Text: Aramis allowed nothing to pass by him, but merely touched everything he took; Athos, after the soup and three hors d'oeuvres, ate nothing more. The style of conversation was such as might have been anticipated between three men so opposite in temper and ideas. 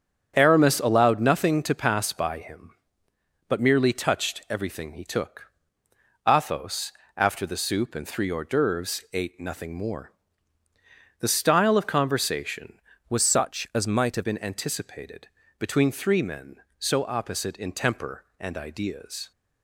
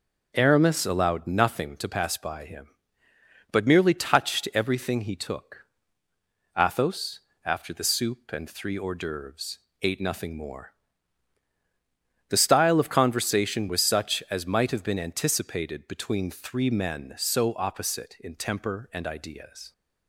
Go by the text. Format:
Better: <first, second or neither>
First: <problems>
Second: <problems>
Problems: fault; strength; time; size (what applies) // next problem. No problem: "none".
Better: second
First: starts louder than the rest; strong; until 1.3 s; 8 dB // changes voice from "was" to "have"; from 13.0 to 14.2 s; 1.2 s long // pauses between "anticipated" and "between"; slight; at 15.2 s; 0.30 s long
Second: starts louder than the rest; noticeable; until 1.3 s; 6 dB